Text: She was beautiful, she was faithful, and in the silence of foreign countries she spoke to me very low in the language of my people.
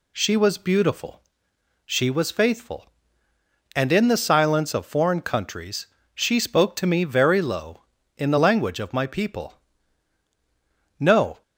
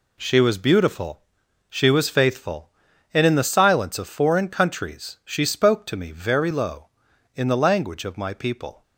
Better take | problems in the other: second | pauses between "countries" and "she"; slight; at 5.8 s; 0.26 s long // goes on to say "No"; slight; from 10.9 s on; 0.42 s long

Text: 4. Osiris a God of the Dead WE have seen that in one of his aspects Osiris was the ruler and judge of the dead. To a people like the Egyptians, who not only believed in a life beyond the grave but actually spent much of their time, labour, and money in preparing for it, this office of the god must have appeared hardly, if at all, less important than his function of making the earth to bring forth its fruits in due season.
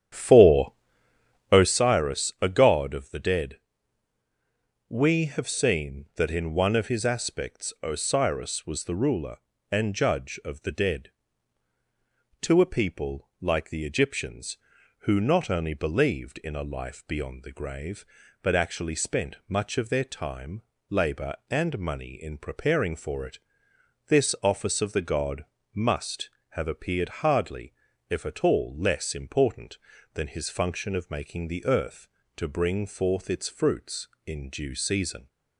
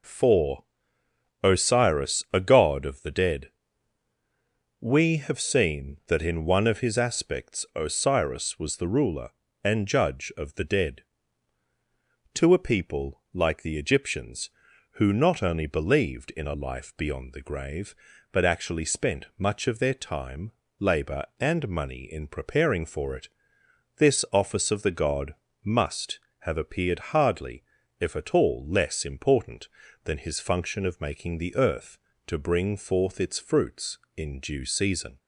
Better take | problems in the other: second | starts louder than the rest; strong; until 1.8 s; 10 dB // pauses between "Dead" and "WE"; strong; at 3.5 s; 1.3 s long; strong in the second // pauses between "god" and "must"; slight; at 25.4 s; 0.28 s long; slight in the second

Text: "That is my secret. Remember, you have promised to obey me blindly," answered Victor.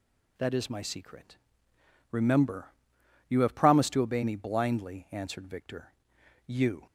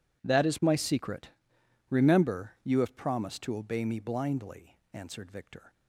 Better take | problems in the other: second | goes on to say "You"; slight; from 6.4 s on; 0.38 s long

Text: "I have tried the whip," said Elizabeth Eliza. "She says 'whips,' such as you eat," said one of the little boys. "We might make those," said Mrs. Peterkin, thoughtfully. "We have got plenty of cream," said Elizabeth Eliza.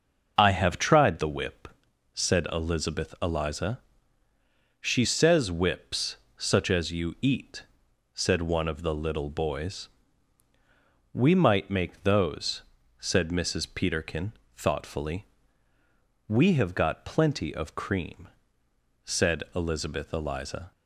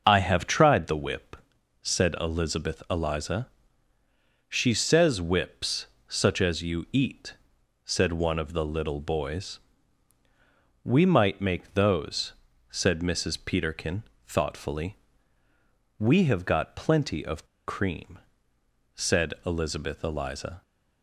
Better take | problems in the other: first | starts louder than the rest; until 1.0 s; 6.5 dB; also in the first // pauses between "of" and "cream"; slight; at 17.4 s; 0.20 s long

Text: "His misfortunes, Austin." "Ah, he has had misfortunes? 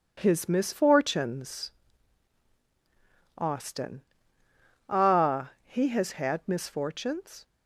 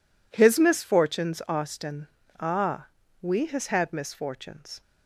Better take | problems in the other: first | says "we" for "he"; at 3.2 s

